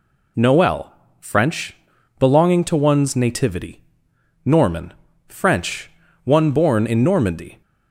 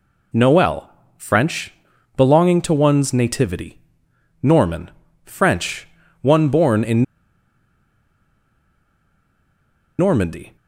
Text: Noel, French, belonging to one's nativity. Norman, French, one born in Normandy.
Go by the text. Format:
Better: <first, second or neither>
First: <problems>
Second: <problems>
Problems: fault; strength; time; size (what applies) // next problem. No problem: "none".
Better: first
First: none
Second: pauses between "in" and "Normandy"; strong; at 7.0 s; 2.9 s long